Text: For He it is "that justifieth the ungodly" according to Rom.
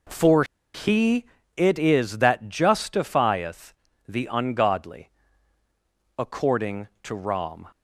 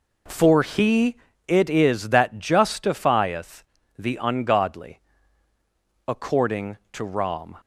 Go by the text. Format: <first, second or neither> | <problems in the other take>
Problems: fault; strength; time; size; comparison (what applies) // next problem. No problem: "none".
second | pauses between "For" and "He"; slight; at 0.4 s; 0.30 s long // pauses between "He" and "it"; slight; at 1.2 s; 0.30 s long; slight in the second // pauses between "justifieth" and "the"; slight; at 3.7 s; 0.34 s long; slight in the second // pauses between "ungodly" and "according"; at 5.0 s; 1.0 s long; also in the second